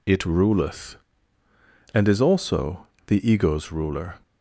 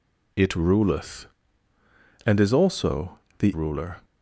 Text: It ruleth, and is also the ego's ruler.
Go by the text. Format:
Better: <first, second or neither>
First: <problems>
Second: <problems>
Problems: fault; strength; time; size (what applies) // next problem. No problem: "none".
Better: first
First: pauses between "also" and "the"; slight; at 2.8 s; 0.18 s long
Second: pauses between "also" and "the"; slight; at 3.1 s; 0.18 s long // skips "ego's"; at 3.5 s